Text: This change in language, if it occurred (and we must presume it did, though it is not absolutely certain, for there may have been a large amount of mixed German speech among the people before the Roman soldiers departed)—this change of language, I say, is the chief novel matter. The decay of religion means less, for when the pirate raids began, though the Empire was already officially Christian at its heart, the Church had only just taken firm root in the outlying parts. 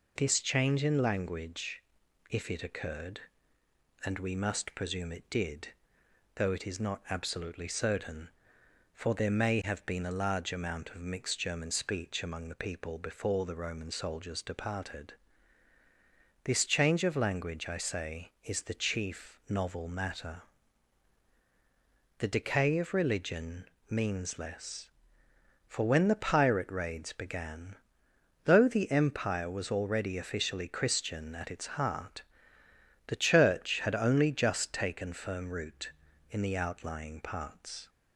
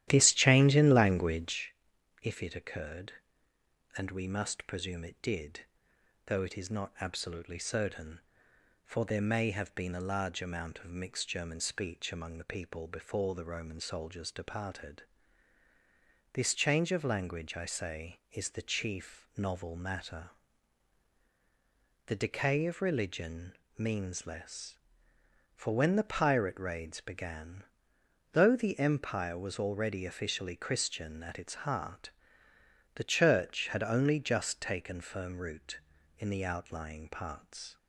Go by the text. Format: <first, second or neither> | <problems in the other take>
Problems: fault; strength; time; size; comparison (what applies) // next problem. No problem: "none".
first | starts louder than the rest; strong; until 1.7 s; 13 dB // pauses between "religion" and "means"; slight; at 23.5 s; 0.20 s long; slight in the first